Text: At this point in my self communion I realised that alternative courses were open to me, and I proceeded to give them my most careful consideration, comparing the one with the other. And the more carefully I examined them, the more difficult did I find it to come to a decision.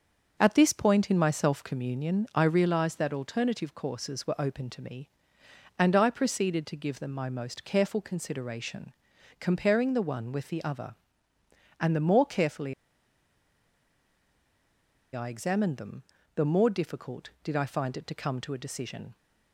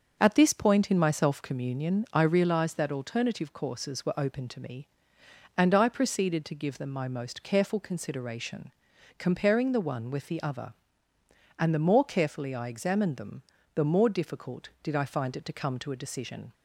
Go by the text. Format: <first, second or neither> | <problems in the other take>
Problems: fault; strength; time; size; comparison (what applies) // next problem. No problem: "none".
second | starts louder than the rest; until 1.4 s; 6.5 dB; also in the second // pauses between "carefully" and "I"; strong; at 12.7 s; 2.4 s long